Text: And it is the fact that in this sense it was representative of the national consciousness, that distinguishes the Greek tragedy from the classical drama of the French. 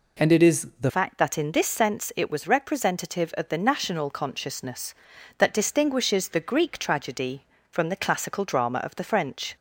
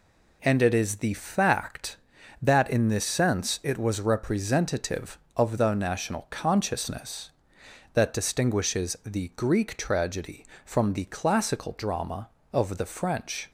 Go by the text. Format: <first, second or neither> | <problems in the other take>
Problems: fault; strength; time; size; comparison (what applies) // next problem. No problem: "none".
second | changes voice at "fact"; from 0.9 s on; 8.6 s long